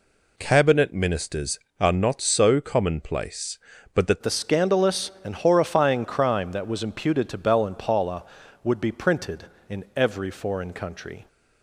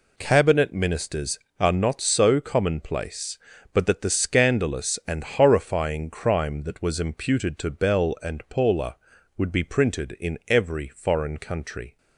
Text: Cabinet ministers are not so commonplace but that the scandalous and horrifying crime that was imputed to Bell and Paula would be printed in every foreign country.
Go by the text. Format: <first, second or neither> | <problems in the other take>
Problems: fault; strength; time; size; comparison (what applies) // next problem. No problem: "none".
second | changes voice at "the"; from 4.2 s on; 7.0 s long